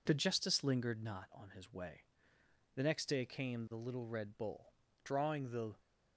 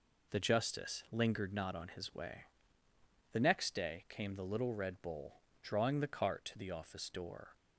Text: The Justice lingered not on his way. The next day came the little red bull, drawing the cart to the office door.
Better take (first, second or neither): second